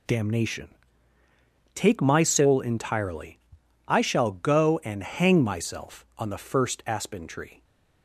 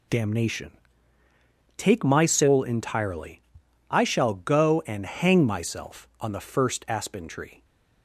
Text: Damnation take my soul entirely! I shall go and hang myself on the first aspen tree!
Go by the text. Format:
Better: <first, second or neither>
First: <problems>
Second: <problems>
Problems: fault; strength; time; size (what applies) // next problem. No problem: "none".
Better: neither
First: pauses between "Damnation" and "take"; at 0.6 s; 1.0 s long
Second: pauses between "Damnation" and "take"; at 0.7 s; 1.0 s long